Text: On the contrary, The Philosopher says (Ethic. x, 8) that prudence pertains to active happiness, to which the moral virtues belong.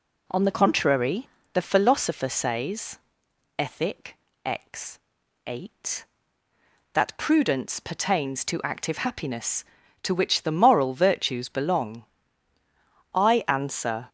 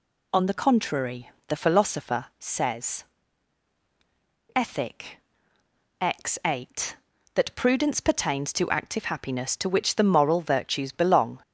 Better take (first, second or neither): second